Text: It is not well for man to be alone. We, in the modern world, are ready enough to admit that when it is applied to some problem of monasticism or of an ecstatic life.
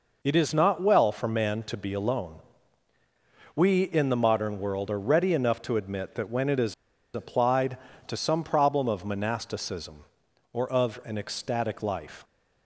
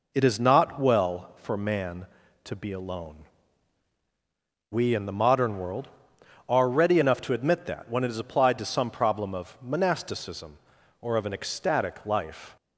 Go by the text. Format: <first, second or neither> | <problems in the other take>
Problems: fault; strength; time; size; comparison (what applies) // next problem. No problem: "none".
second | pauses between "is" and "applied"; at 6.7 s; 0.41 s long